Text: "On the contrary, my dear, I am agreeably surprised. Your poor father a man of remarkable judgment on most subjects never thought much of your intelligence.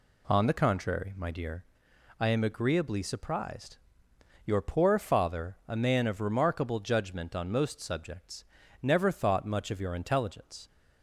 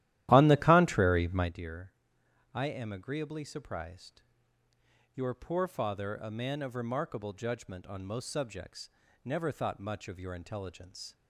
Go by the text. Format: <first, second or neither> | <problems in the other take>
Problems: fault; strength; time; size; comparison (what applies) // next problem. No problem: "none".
first | starts louder than the rest; strong; until 1.5 s; 14 dB // pauses between "subjects" and "never"; slight; at 8.9 s; 0.34 s long; also in the first